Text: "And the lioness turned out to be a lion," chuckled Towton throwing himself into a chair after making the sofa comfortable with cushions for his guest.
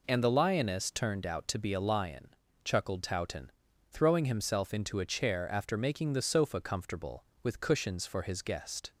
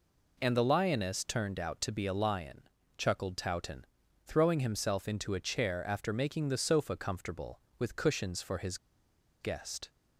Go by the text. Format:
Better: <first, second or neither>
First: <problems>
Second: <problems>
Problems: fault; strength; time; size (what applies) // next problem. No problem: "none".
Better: first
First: pauses between "Towton" and "throwing"; at 3.4 s; 0.38 s long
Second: pauses between "Towton" and "throwing"; at 3.8 s; 0.38 s long // pauses between "his" and "guest"; noticeable; at 8.7 s; 0.64 s long